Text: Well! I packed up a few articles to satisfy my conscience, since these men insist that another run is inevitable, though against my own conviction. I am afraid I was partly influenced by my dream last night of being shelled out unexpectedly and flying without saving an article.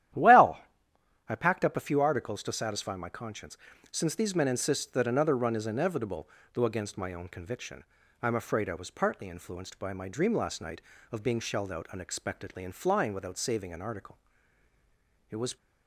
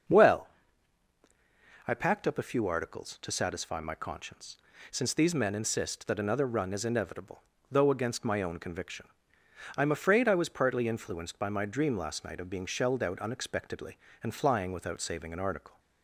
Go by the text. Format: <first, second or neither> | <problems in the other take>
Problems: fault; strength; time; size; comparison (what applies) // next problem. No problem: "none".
second | starts louder than the rest; strong; until 1.8 s; 12 dB; also in the second // goes on to say "It was"; slight; from 15.3 s on; 0.26 s long